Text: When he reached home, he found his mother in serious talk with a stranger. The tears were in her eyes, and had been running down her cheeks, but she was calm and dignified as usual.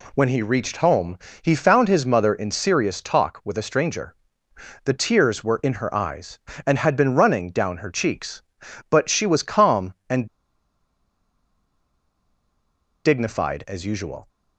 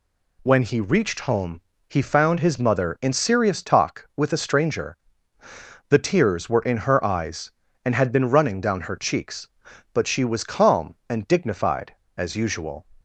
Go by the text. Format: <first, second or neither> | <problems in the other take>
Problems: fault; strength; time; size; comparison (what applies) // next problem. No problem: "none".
second | pauses between "and" and "dignified"; strong; at 10.2 s; 2.7 s long